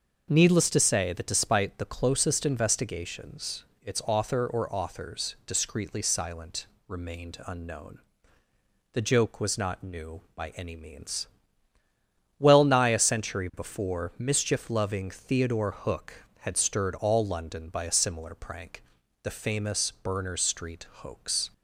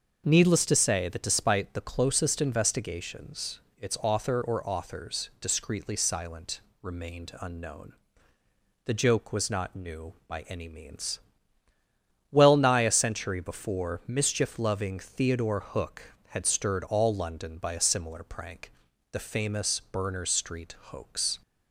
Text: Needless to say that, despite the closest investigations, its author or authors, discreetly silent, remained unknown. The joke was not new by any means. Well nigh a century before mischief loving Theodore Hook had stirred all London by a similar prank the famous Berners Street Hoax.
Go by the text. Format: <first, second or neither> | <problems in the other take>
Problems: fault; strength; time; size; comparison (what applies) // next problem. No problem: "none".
neither | starts louder than the rest; the same in both // pauses between "prank" and "the"; the same in both